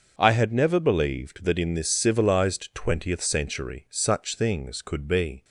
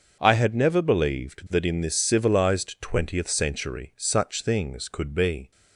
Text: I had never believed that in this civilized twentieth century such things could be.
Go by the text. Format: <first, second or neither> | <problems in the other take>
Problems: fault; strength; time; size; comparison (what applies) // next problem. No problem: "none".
neither | starts louder than the rest; the same in both